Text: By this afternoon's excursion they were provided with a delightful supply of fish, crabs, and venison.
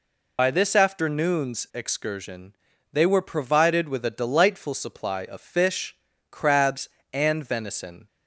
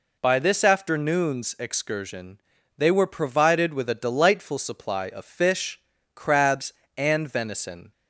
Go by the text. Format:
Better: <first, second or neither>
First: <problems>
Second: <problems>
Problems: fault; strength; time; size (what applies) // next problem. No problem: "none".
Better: second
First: loses the start of "By"; at 0.3 s; 80 ms // pauses between "excursion" and "they"; at 2.5 s; 0.38 s long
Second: pauses between "excursion" and "they"; at 2.3 s; 0.38 s long